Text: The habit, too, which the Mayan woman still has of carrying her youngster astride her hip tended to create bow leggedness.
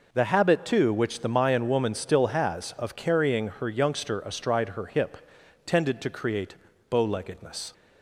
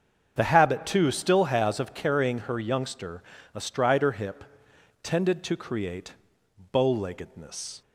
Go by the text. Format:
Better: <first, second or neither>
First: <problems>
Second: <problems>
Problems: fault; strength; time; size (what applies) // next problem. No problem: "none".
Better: first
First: pauses between "hip" and "tended"; noticeable; at 5.1 s; 0.48 s long // pauses between "create" and "bow"; slight; at 6.5 s; 0.34 s long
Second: starts louder than the rest; until 1.3 s; 7 dB // skips "which the Mayan woman"; at 1.0 s // pauses between "youngster" and "astride"; slight; at 3.2 s; 0.32 s long // pauses between "hip" and "tended"; noticeable; at 4.4 s; 0.58 s long // pauses between "create" and "bow"; noticeable; at 6.1 s; 0.58 s long